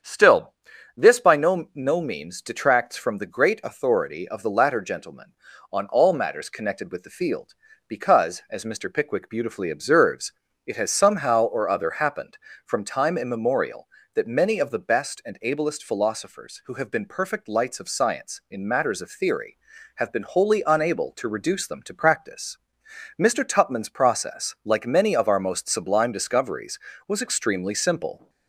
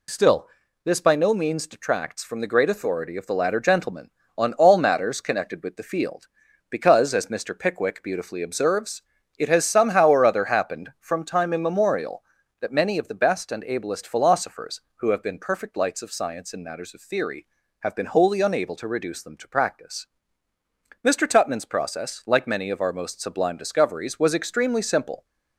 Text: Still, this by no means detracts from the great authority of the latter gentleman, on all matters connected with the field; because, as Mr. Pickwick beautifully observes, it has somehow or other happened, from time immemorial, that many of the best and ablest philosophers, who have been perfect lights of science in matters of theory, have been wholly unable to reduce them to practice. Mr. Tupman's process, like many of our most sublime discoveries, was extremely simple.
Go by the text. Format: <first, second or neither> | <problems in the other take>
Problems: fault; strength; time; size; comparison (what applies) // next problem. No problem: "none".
second | starts louder than the rest; strong; until 1.4 s; 8 dB // says "no" twice; at 1.7 s